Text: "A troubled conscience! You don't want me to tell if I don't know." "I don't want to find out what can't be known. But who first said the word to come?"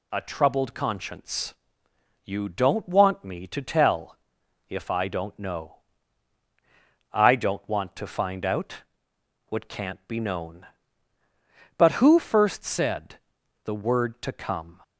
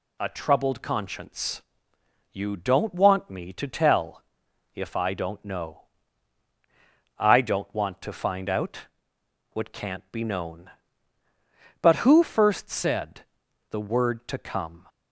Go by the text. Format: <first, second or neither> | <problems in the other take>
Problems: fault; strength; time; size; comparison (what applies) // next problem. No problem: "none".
neither | pauses between "tell" and "if"; noticeable; the same in both // pauses between "out" and "what"; noticeable; the same in both // pauses between "said" and "the"; the same in both